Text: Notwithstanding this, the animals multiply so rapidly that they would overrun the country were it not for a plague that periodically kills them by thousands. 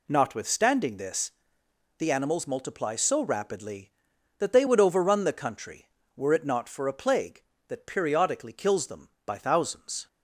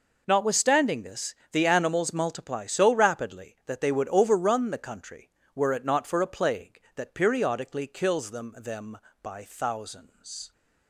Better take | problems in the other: first | says "them" twice; at 8.5 s

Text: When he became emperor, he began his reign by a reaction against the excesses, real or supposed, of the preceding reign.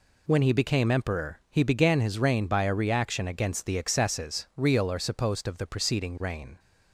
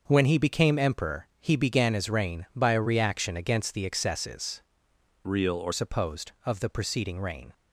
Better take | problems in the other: first | starts louder than the rest; noticeable; until 1.0 s; 6 dB // changes voice from "real" to "or"; from 5.2 to 5.7 s; 0.5 s long

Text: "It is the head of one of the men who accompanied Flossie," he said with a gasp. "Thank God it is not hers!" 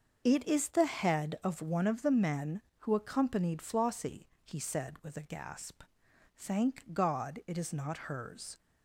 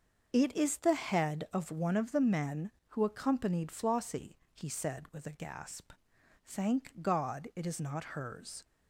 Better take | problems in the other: neither | starts louder than the rest; the same in both // pauses between "not" and "hers"; slight; the same in both

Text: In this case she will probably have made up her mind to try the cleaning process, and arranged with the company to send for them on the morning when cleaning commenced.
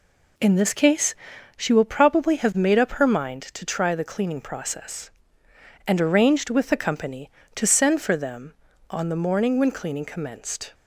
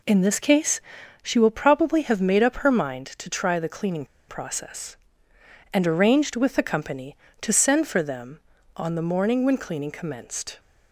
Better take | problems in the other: first | pauses between "case" and "she"; at 0.7 s; 0.42 s long; also in the first // pauses between "cleaning" and "process"; slight; at 4.0 s; 0.24 s long

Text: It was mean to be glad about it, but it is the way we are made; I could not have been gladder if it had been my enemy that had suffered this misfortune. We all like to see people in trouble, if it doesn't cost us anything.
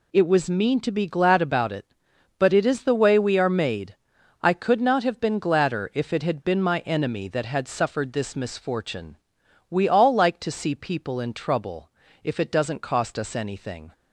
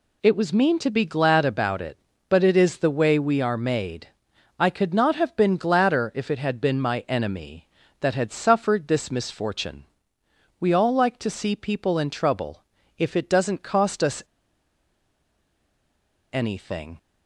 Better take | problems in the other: first | pauses between "us" and "anything"; strong; at 14.2 s; 2.1 s long

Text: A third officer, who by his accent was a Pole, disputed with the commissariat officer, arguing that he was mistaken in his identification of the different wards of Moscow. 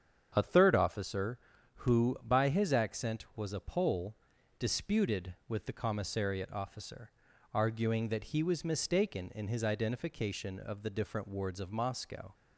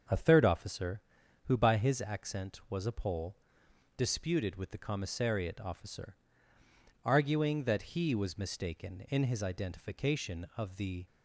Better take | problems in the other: first | starts louder than the rest; until 1.5 s; 7 dB; strong in the first // stops before "different wards of Moscow"; at 11.0 s

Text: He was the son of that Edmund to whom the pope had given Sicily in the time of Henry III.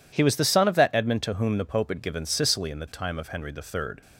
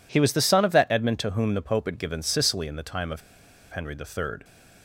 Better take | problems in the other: first | pauses between "of" and "Henry"; noticeable; at 3.2 s; 0.51 s long

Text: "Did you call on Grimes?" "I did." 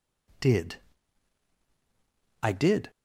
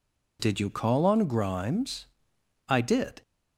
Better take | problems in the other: second | skips "you call on Grimes"; at 1.5 s

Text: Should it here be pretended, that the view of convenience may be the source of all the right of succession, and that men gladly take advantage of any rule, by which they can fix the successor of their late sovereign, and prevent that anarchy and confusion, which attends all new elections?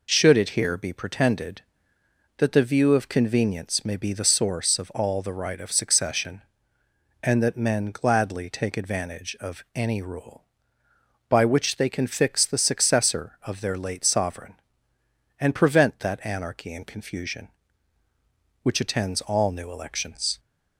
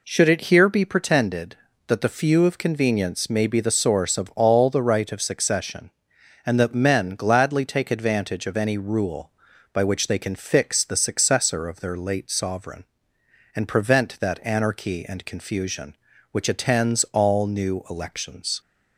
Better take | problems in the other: first | says "few" for "view"; at 2.0 s

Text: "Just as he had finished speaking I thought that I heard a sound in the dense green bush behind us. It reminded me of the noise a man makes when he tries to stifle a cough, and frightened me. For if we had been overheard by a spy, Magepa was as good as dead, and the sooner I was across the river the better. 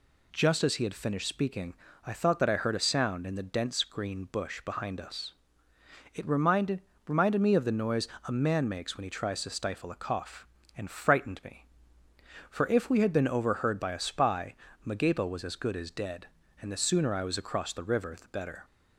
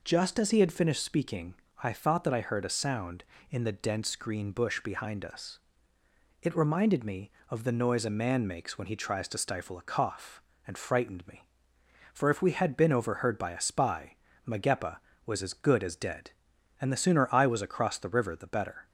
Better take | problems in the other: second | pauses between "speaking" and "I"; slight; at 1.7 s; 0.30 s long; slight in the second // says "reminded" twice; at 7.0 s // pauses between "noise" and "a"; slight; at 8.0 s; 0.18 s long

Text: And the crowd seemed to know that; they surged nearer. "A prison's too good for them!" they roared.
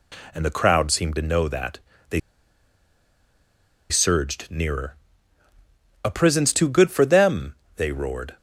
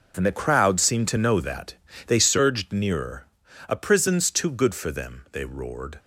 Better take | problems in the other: second | pauses between "they" and "surged"; strong; at 2.1 s; 1.7 s long

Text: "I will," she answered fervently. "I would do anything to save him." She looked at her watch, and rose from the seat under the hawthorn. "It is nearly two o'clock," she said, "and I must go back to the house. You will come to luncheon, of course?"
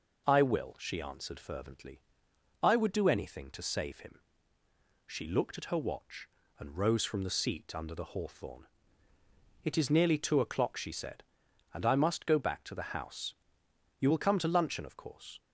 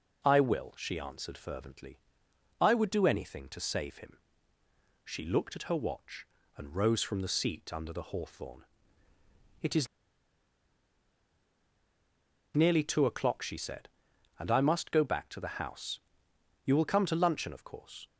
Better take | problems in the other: first | pauses between "is" and "nearly"; strong; at 9.8 s; 2.6 s long

